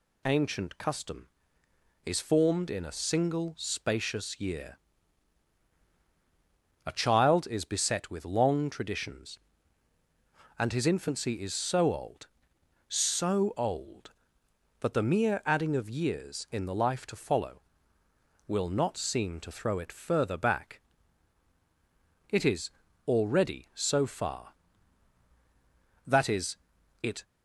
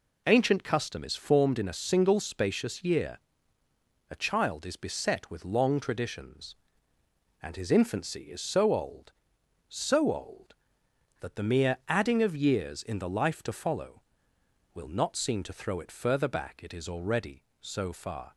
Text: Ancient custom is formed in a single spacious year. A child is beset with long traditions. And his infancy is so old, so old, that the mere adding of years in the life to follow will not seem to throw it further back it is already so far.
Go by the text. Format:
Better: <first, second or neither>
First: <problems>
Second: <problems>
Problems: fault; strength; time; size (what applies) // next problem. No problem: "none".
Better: second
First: pauses between "back" and "it"; strong; at 20.8 s; 1.5 s long // pauses between "is" and "already"; at 22.6 s; 0.38 s long // goes on to say "That is it"; noticeable; from 26.0 s on; 1.1 s long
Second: none